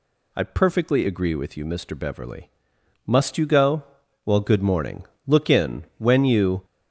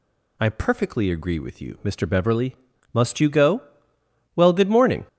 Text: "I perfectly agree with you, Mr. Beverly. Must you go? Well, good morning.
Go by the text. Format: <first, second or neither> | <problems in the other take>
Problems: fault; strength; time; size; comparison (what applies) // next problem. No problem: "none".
second | goes on to say "Look in when you"; from 5.2 s on; 1.4 s long